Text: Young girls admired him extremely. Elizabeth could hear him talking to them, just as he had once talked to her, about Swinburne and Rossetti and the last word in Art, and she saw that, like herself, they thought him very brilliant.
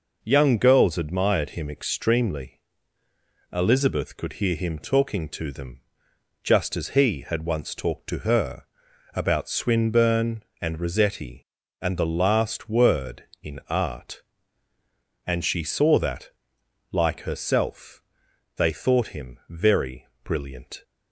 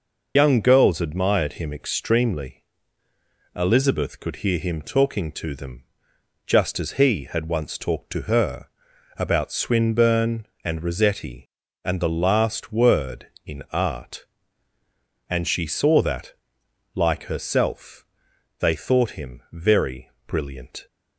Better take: first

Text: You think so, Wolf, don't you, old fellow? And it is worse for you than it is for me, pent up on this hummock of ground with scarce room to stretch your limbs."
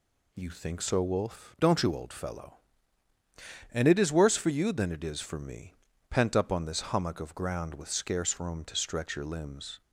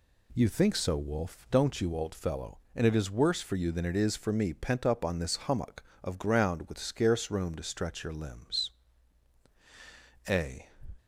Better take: first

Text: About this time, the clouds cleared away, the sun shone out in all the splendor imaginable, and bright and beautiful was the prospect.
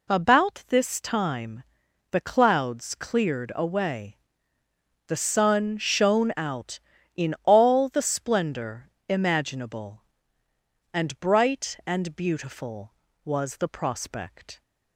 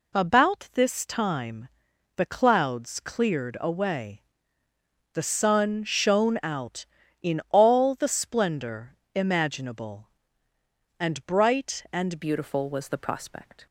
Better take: first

